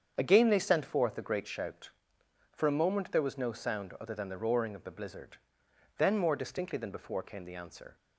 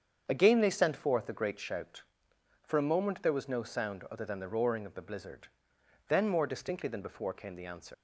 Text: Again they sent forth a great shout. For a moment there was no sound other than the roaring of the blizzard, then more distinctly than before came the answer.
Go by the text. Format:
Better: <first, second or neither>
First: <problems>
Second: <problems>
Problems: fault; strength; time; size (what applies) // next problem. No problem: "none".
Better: first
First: starts louder than the rest; strong; until 1.1 s; 7.5 dB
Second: starts louder than the rest; strong; until 1.2 s; 7.5 dB // leaves "answer" unfinished; at 7.9 s; 115 ms